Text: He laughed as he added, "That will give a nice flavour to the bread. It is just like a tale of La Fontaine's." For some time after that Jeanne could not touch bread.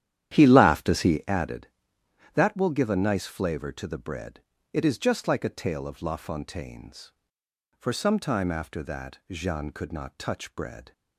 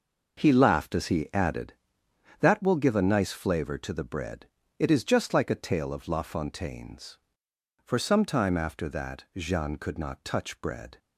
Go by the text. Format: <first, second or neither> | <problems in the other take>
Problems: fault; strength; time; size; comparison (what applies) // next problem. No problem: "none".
second | starts louder than the rest; strong; until 1.3 s; 11 dB